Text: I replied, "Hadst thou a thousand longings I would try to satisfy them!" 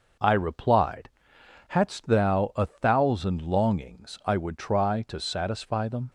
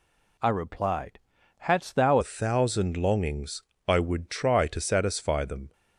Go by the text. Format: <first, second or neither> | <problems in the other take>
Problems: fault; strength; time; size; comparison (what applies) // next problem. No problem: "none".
first | changes voice at "a"; from 2.2 s on; 3.5 s long // pauses between "longings" and "I"; slight; at 3.6 s; 0.24 s long